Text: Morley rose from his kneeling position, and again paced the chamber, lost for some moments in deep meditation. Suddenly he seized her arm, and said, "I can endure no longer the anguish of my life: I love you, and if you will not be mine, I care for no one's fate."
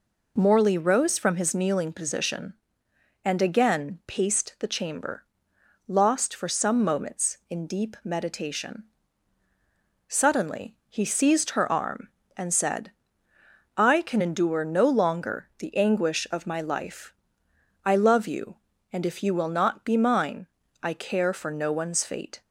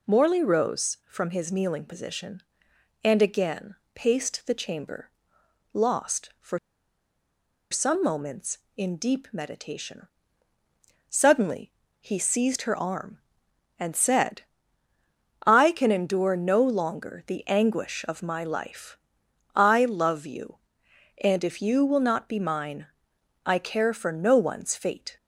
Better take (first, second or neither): first